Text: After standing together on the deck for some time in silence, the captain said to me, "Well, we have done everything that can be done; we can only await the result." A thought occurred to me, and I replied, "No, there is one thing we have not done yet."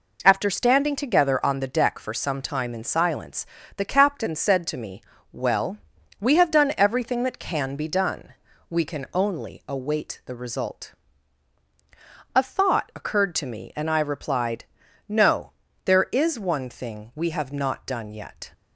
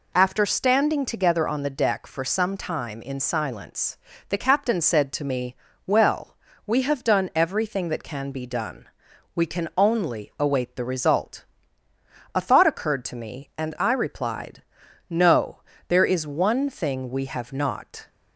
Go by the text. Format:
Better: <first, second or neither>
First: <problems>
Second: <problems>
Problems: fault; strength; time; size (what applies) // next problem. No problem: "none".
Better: first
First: none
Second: stops before "done yet"; at 18.0 s